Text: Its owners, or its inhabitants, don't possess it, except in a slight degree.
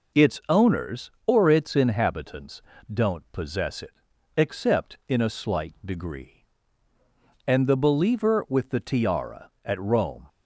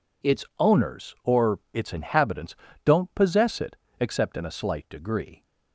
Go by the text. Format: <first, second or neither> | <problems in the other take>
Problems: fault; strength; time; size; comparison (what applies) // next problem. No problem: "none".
second | goes on to say "And the believer with the tiara at Rome"; strong; from 7.4 s on; 2.8 s long